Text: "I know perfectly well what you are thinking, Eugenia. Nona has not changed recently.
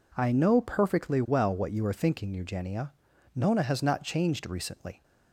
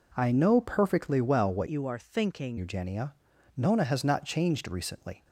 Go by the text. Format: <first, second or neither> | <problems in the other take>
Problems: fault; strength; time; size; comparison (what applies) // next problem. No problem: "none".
first | changes voice from "you" to "thinking"; from 1.6 to 2.5 s; 0.9 s long